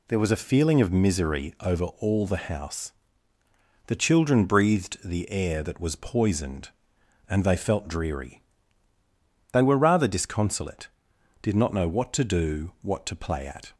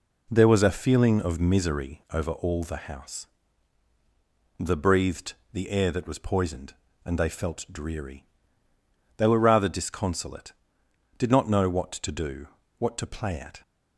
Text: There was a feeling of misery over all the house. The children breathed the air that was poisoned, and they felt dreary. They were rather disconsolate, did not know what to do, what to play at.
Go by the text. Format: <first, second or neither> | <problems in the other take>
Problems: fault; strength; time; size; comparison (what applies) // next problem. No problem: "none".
first | skips "children"; at 4.7 s // pauses between "breathed" and "the"; slight; at 5.3 s; 0.20 s long